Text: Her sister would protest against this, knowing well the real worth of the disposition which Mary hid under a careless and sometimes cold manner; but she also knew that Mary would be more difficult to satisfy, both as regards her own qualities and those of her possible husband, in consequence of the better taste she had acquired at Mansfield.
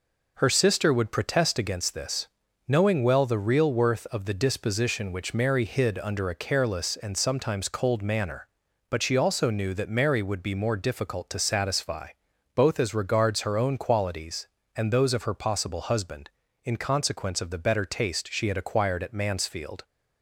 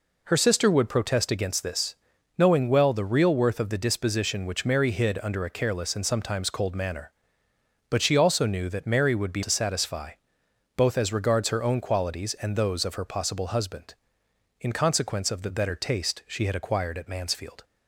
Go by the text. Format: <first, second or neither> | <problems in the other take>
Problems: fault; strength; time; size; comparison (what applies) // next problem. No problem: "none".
first | skips "more difficult"; at 9.4 s